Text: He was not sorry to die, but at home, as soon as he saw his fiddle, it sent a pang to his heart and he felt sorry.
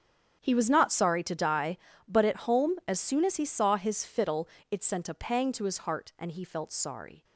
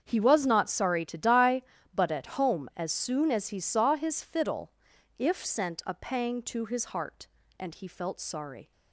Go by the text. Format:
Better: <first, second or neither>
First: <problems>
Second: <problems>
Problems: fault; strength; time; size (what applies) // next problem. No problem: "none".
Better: first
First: starts louder than the rest; strong; until 1.4 s; 8 dB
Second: starts louder than the rest; strong; until 1.0 s; 7.5 dB // says "if" for "it"; at 5.1 s